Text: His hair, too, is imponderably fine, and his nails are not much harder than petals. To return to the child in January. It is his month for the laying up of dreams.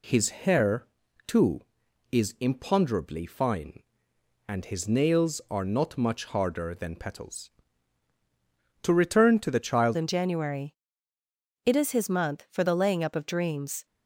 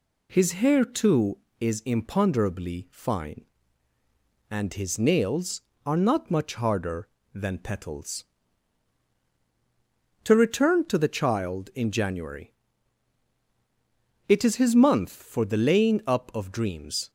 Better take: second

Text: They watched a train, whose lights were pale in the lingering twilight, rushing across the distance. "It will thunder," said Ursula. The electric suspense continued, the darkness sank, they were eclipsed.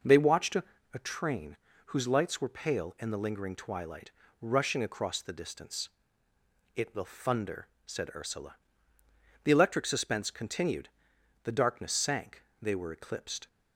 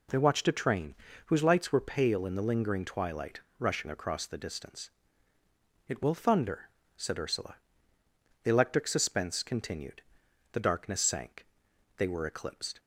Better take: second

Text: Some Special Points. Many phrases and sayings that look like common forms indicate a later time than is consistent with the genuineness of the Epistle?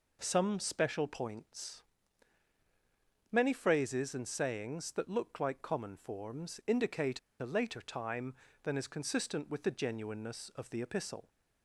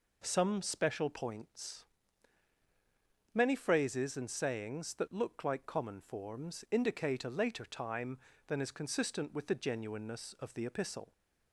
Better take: second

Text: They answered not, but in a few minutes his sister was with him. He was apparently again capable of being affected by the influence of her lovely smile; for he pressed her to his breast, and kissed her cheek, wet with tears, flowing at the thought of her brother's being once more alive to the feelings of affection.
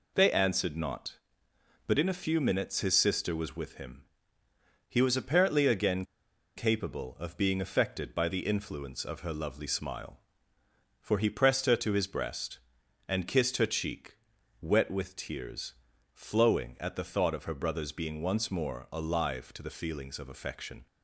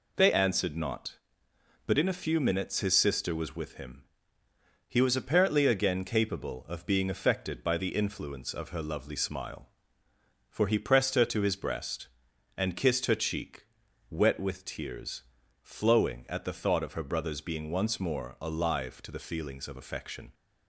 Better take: second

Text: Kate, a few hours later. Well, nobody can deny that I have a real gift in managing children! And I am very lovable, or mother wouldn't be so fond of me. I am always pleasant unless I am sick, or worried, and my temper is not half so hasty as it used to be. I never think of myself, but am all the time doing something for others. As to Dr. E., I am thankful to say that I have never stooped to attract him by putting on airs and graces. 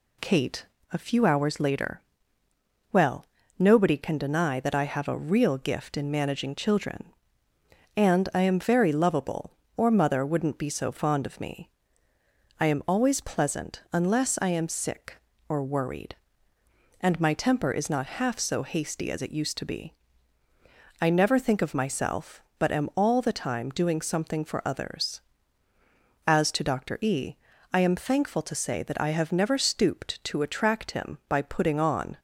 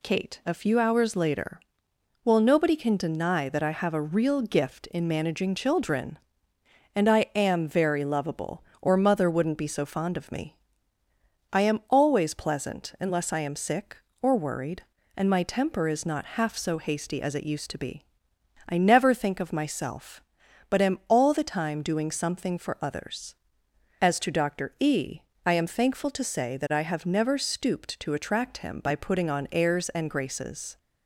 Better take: second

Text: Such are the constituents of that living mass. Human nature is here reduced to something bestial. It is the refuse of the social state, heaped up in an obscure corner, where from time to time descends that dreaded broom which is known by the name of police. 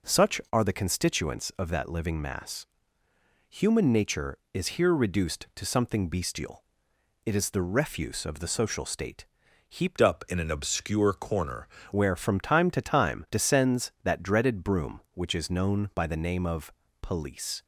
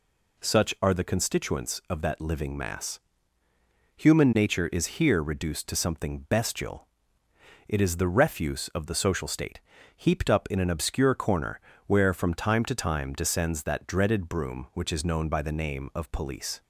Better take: second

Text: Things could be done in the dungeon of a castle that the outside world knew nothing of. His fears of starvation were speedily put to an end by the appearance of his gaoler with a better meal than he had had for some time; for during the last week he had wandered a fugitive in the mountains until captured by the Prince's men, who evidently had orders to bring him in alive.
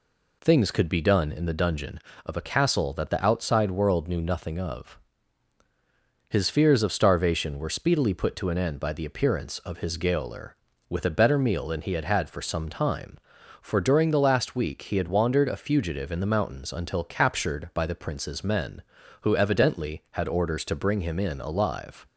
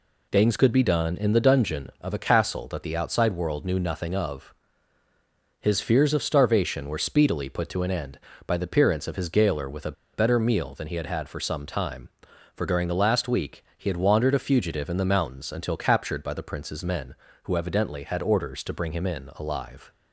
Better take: first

